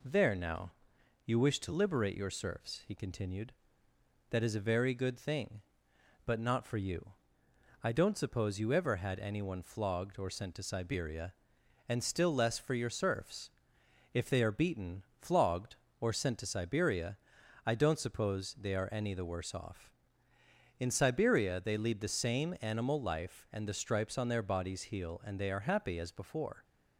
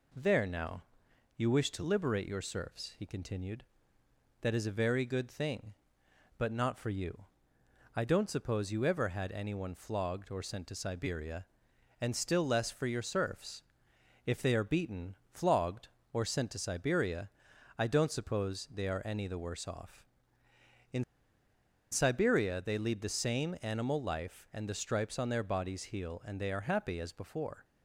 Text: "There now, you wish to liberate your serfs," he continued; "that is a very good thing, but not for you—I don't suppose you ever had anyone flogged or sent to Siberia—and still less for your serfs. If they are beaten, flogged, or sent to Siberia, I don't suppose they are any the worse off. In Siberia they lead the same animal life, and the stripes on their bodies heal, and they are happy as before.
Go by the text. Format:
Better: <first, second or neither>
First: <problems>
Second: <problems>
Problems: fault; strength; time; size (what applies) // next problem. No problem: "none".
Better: first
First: none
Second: pauses between "In" and "Siberia"; noticeable; at 21.0 s; 0.88 s long